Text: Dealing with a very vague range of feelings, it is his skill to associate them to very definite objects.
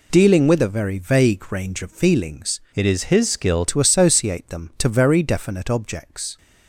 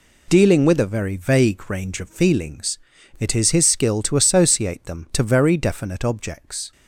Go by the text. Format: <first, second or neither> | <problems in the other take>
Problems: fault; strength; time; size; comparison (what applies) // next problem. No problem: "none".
second | changes voice from "it" to "skill"; from 2.7 to 3.6 s; 0.9 s long